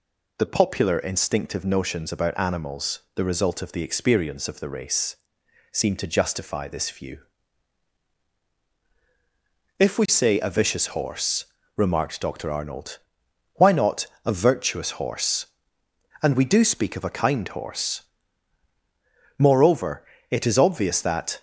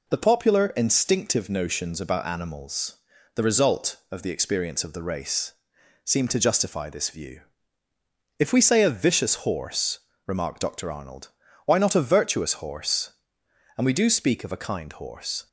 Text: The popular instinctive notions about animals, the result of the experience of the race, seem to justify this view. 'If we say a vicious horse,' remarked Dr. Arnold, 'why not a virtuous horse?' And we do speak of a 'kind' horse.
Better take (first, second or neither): second